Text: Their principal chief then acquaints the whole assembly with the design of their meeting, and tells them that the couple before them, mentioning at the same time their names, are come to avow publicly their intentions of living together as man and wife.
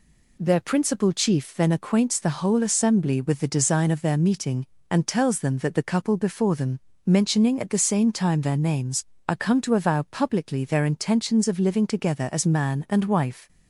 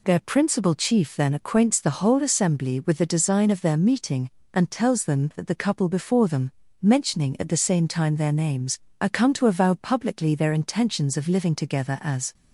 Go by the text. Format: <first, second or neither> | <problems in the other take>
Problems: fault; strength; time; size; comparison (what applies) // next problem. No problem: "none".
first | stops before "man and wife"; at 12.3 s